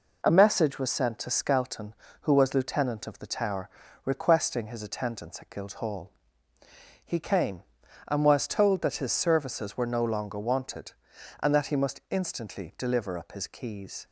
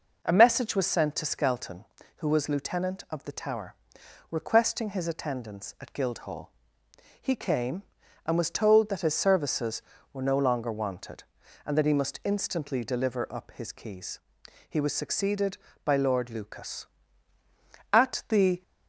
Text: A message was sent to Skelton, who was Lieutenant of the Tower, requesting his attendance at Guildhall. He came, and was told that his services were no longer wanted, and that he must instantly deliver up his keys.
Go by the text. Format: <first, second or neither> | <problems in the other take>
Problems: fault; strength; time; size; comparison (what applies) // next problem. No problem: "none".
first | goes on to say "He was succeeded by Lord Lucas At the"; strong; from 14.6 s on; 3.9 s long